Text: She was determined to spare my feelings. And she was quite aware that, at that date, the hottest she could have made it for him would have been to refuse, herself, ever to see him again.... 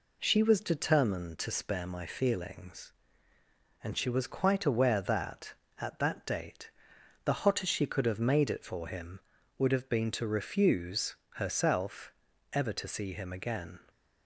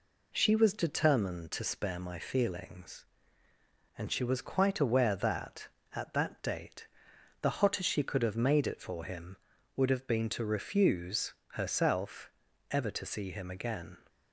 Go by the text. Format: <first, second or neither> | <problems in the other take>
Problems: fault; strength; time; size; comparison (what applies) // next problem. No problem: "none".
neither | none